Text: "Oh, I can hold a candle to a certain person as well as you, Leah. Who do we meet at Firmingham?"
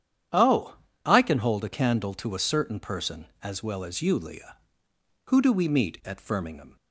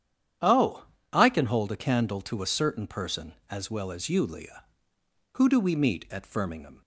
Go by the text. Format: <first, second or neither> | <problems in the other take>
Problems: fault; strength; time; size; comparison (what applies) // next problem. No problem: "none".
neither | starts louder than the rest; strong; the same in both